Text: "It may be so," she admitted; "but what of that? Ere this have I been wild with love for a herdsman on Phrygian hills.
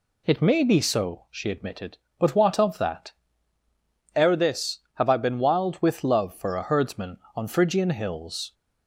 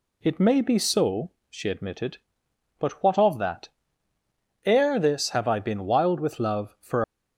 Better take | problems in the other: first | stops before "a herdsman on Phrygian hills"; at 7.0 s

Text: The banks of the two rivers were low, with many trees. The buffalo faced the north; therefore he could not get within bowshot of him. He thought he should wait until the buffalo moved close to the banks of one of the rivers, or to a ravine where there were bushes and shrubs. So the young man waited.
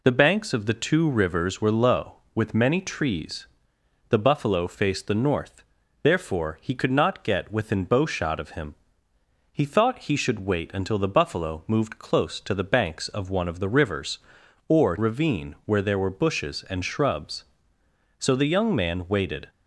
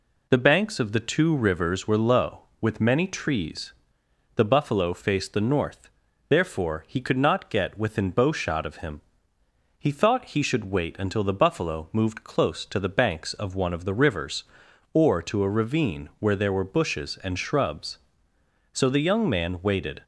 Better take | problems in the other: second | skips "to a"; at 14.9 s

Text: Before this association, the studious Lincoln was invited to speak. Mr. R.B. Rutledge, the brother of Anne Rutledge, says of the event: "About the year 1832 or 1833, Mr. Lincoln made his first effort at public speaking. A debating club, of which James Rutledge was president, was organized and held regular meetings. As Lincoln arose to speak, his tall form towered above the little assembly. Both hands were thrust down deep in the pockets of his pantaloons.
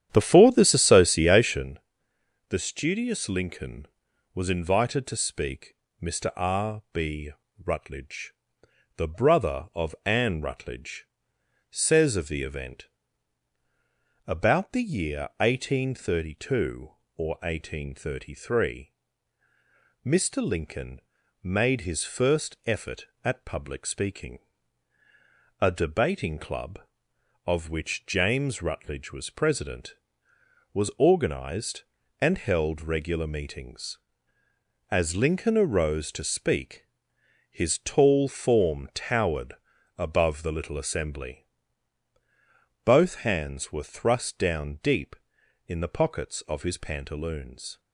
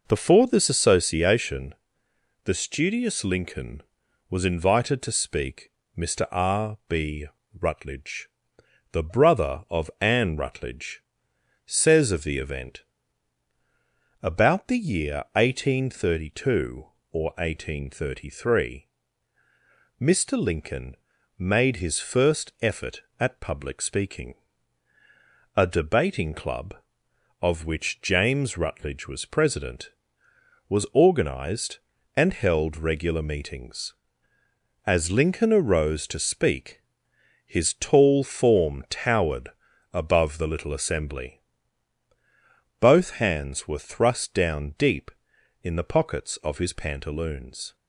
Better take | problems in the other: second | starts louder than the rest; strong; until 1.7 s; 10 dB // pauses between "Lincoln" and "made"; at 21.0 s; 0.42 s long; also in the second // pauses between "towered" and "above"; at 39.5 s; 0.44 s long; also in the second

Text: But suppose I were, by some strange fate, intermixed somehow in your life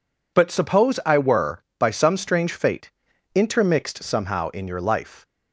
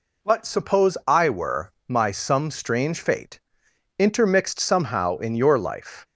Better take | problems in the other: first | says "my" for "by"; at 1.8 s

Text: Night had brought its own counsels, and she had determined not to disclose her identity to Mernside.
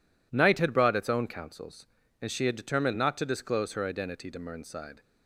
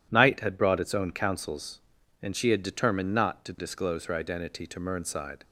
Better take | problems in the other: neither | none

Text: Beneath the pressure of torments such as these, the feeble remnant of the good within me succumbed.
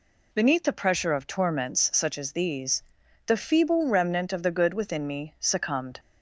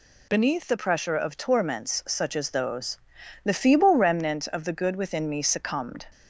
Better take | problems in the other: first | says "those" for "these"; at 2.4 s

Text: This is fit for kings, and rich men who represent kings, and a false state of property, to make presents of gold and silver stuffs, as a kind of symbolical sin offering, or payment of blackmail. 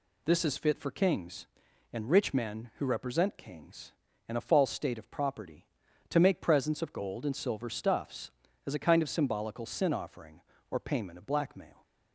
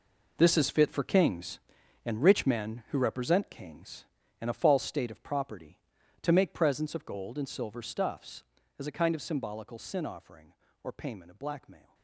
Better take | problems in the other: first | gets quieter; strong; throughout; 13 dB

